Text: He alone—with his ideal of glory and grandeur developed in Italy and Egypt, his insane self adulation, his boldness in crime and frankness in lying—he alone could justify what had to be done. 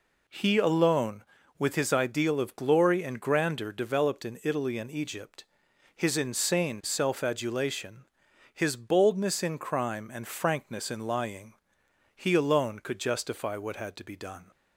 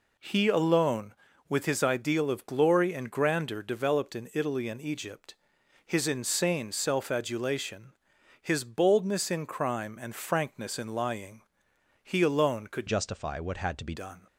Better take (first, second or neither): first